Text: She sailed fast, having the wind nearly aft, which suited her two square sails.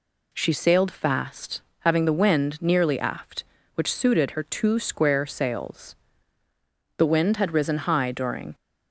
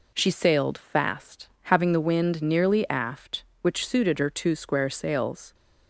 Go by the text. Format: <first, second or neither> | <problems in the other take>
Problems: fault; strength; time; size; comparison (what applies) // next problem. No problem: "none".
second | goes on to say "The wind had risen high during"; from 6.9 s on; 1.5 s long